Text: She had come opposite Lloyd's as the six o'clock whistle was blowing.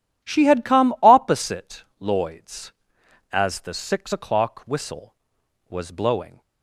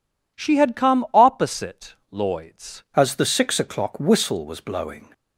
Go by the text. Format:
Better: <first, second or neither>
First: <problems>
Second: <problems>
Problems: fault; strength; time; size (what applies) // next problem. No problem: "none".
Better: first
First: pauses between "opposite" and "Lloyd's"; slight; at 1.8 s; 0.16 s long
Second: pauses between "opposite" and "Lloyd's"; slight; at 1.9 s; 0.16 s long // changes voice at "as"; from 2.9 s on; 2.1 s long